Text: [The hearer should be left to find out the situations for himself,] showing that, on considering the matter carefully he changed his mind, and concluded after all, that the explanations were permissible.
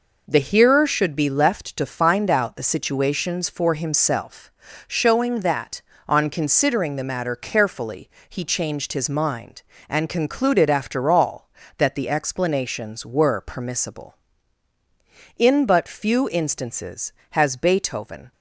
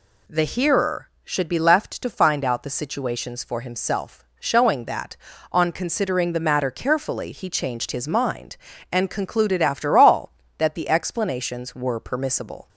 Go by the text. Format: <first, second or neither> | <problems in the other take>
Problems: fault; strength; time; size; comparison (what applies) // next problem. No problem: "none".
second | pauses between "carefully" and "he"; slight; at 8.0 s; 0.20 s long // goes on to say "In but few instances has Beethoven"; strong; from 15.3 s on; 2.9 s long